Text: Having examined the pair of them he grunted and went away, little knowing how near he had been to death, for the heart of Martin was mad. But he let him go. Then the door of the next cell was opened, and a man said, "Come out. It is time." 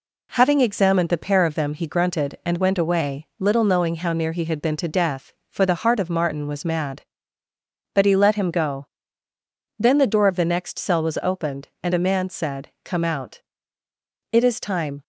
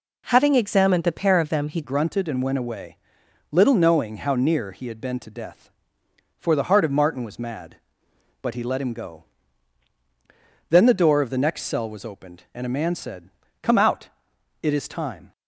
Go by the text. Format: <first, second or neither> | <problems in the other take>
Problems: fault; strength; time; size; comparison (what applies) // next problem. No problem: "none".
first | changes voice at "grunted"; from 1.8 s on; 13.5 s long